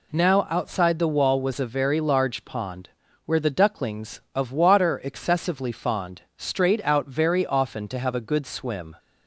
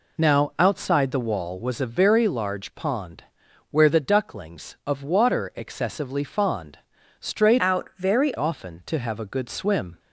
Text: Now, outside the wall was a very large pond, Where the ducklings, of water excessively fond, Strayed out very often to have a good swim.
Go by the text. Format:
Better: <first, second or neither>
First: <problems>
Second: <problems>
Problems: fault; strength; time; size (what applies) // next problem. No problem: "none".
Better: first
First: none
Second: changes voice from "out" to "very"; from 7.5 to 8.3 s; 0.8 s long